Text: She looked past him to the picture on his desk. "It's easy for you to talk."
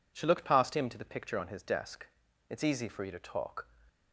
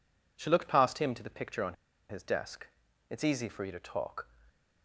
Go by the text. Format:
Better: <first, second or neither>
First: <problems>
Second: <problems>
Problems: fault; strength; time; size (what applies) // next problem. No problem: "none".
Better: first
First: none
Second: pauses between "on" and "his"; at 1.7 s; 0.36 s long